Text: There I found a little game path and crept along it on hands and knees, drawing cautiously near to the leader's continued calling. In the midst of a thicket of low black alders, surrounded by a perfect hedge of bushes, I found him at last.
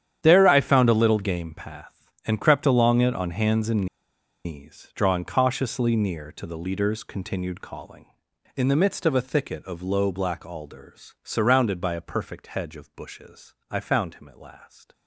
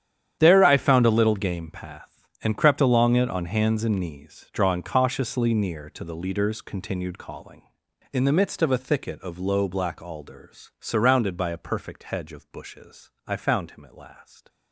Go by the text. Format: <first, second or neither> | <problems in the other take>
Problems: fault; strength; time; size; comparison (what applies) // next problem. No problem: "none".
second | starts louder than the rest; strong; until 1.2 s; 9.5 dB; strong in the second // pauses between "and" and "knees"; noticeable; at 3.8 s; 0.59 s long